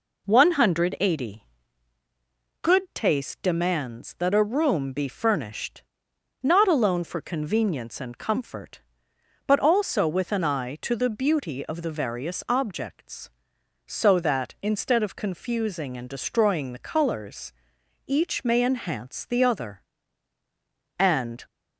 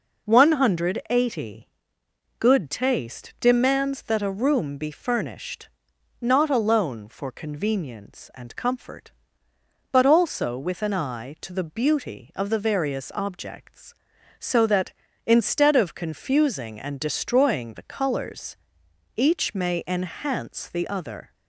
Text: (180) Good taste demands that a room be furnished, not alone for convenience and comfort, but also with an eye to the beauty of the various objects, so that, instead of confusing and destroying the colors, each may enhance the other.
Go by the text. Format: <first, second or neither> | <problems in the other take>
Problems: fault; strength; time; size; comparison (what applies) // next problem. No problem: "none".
second | goes on to say "And"; slight; from 20.9 s on; 0.48 s long